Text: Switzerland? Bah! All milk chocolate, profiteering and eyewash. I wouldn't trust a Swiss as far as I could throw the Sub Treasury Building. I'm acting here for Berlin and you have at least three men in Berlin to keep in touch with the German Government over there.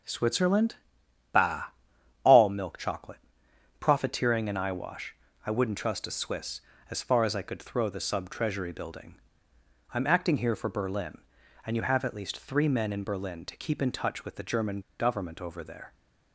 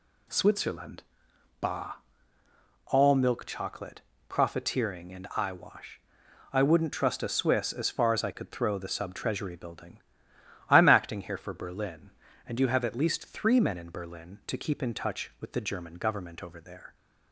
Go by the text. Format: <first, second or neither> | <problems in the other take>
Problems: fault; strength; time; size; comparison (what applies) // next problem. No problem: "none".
second | pauses between "German" and "Government"; slight; at 14.8 s; 0.18 s long